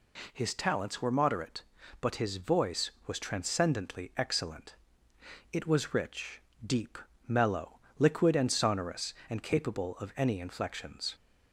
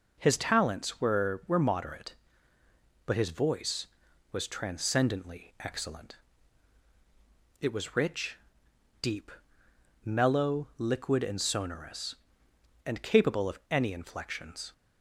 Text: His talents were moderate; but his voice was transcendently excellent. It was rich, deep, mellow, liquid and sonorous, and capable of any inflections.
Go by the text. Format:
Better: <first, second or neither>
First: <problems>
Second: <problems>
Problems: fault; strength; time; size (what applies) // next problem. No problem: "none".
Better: first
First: none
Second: says "were" twice; at 1.4 s